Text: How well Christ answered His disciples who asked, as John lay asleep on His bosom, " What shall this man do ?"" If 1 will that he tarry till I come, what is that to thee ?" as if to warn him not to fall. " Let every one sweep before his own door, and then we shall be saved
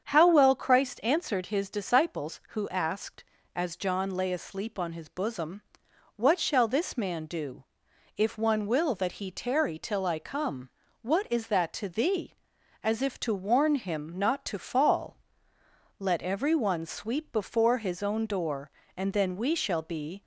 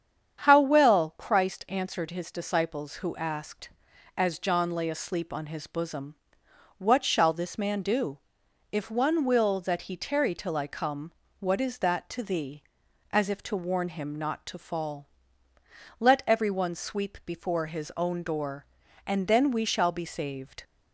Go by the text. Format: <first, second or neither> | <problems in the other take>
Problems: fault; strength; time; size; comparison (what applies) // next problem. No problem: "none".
second | starts louder than the rest; strong; until 1.0 s; 8 dB; strong in the second // stops before "saved"; at 20.2 s